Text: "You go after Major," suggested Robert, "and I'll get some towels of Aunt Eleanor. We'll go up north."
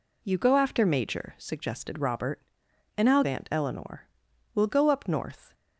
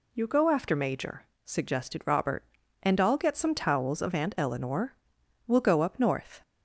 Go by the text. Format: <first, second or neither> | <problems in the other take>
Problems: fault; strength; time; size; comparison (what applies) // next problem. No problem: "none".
second | skips "get some towels of"; at 3.2 s